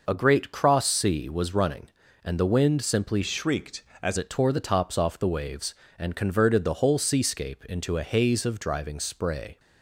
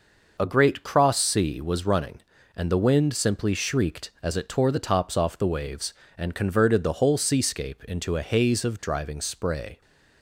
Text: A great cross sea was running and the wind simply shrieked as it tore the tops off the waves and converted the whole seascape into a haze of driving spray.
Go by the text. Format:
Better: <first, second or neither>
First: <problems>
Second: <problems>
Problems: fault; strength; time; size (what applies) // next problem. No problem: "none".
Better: second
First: changes voice from "shrieked" to "as"; from 3.2 to 4.1 s; 0.9 s long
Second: none